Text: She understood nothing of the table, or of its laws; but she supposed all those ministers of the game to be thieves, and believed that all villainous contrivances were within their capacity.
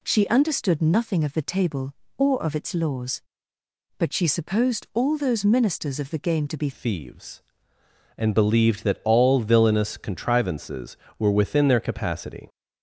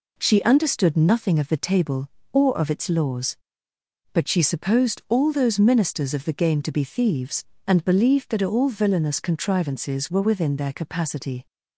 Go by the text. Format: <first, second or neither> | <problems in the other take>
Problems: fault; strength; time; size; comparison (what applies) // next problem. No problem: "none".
second | changes voice at "thieves"; from 6.7 s on; 5.7 s long